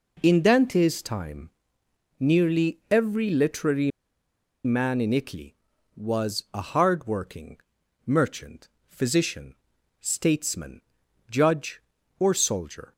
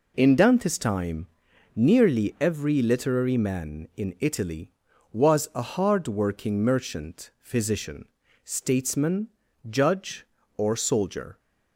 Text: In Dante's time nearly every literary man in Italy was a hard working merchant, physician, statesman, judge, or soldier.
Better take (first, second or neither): second